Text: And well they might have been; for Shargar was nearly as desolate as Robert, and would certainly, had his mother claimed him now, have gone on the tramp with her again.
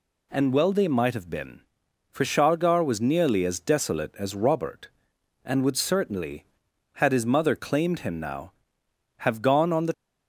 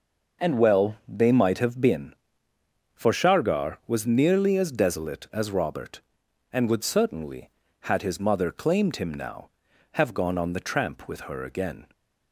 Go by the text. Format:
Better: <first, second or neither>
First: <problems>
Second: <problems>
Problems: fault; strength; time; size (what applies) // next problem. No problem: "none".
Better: second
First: stops before "tramp with her again"; at 9.9 s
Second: none